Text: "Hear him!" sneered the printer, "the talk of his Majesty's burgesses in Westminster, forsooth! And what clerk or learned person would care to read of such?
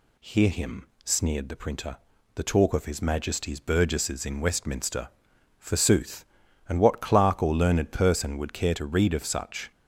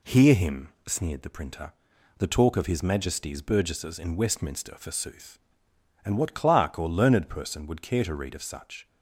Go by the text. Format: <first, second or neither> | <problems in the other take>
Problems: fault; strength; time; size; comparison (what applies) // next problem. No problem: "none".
neither | none